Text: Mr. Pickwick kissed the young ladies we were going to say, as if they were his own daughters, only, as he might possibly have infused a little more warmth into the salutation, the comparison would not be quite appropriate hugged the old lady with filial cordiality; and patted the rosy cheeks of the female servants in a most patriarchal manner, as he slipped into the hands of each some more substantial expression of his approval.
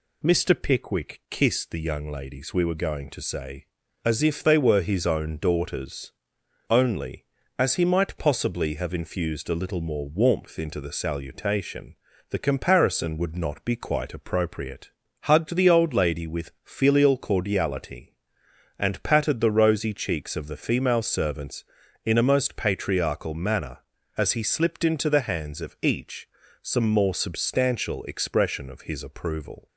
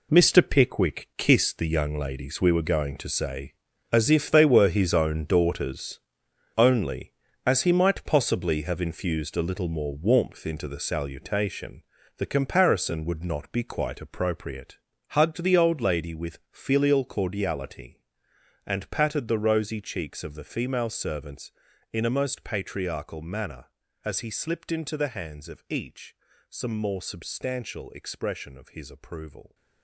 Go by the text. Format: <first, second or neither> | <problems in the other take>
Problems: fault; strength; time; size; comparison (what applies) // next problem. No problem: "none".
first | gets quieter; strong; throughout; 11 dB // pauses between "appropriate" and "hugged"; slight; at 14.7 s; 0.34 s long; slight in the first // pauses between "each" and "some"; slight; at 26.1 s; 0.34 s long; slight in the first